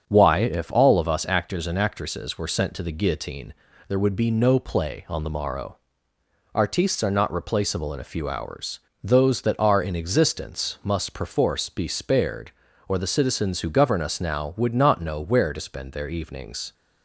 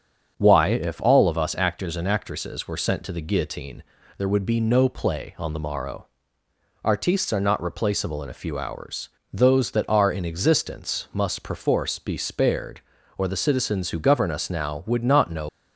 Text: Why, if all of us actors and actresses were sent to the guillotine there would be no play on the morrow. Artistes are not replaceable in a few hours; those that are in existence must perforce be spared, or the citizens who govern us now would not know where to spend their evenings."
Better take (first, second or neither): first